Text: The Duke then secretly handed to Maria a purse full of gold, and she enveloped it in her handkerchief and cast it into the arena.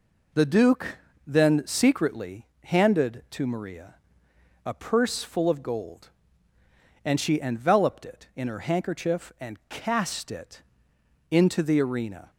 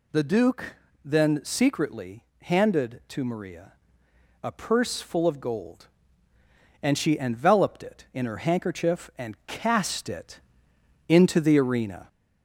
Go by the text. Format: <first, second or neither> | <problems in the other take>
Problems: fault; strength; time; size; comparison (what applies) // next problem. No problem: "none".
first | gets louder; slight; throughout; 2.5 dB // pauses between "Duke" and "then"; slight; at 0.7 s; 0.28 s long; slight in the first // pauses between "secretly" and "handed"; slight; at 2.2 s; 0.18 s long; slight in the first // pauses between "Maria" and "a"; noticeable; at 3.7 s; 0.68 s long; noticeable in the first // pauses between "it" and "into"; noticeable; at 10.3 s; 0.68 s long; noticeable in the first